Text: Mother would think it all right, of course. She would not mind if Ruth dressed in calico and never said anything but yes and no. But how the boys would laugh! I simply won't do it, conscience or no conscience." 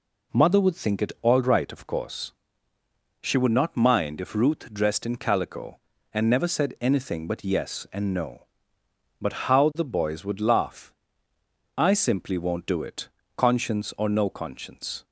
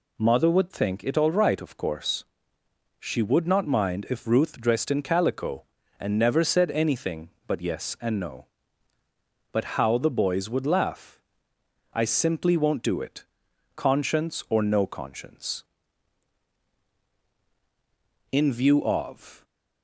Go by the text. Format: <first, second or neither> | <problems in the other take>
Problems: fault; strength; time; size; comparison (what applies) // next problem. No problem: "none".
first | goes on to say "In view of"; noticeable; from 18.3 s on; 1.1 s long